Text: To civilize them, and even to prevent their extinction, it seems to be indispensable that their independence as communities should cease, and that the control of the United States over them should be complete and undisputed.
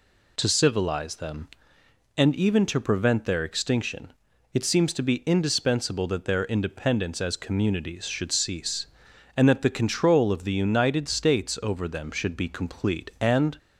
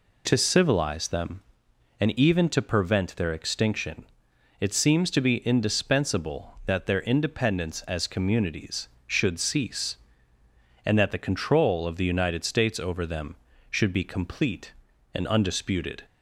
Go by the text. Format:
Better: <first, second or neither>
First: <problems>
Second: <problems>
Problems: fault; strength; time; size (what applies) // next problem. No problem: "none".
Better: second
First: stops before "undisputed"; at 13.5 s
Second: none